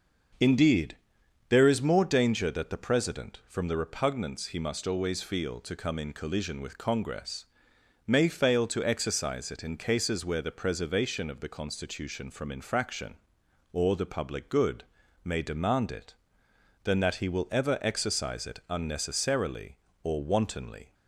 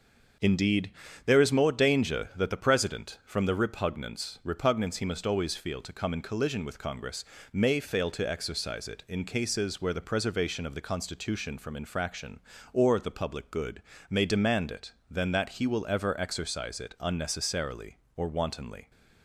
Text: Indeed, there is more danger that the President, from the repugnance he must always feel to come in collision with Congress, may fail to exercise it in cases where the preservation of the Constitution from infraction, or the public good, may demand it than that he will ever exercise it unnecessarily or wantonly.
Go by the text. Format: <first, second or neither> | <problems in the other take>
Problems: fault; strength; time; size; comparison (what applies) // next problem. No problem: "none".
first | starts louder than the rest; until 1.7 s; 6.5 dB; also in the first // says "repugnance" twice; at 4.4 s